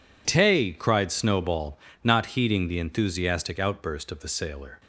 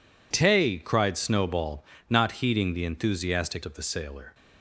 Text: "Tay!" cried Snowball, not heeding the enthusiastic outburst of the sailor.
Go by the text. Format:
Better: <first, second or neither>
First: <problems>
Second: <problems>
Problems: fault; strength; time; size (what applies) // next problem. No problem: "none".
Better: first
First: none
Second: skips "outburst"; at 3.6 s